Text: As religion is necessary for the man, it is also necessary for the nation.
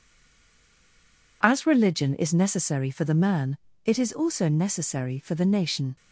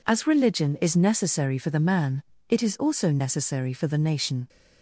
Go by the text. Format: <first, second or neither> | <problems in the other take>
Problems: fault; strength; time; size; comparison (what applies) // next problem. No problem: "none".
second | stays silent before the first word; noticeable; until 1.4 s; 1.4 s long